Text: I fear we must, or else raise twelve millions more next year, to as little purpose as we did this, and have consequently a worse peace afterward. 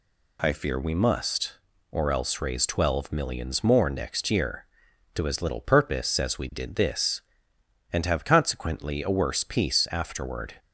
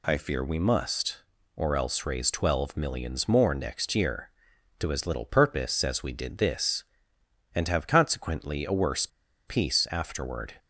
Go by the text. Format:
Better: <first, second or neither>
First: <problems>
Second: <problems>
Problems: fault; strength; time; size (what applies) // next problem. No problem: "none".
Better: first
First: none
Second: pauses between "worse" and "peace"; at 9.0 s; 0.40 s long